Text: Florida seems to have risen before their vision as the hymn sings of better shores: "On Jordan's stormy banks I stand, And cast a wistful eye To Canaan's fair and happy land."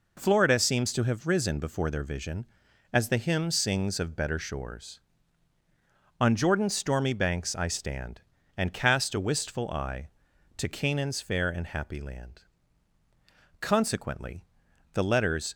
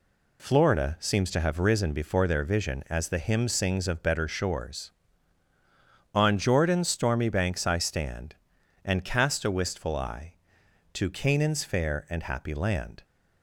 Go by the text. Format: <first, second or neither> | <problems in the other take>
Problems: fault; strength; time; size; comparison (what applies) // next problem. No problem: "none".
second | goes on to say "Consequently the letters"; strong; from 13.5 s on; 1.9 s long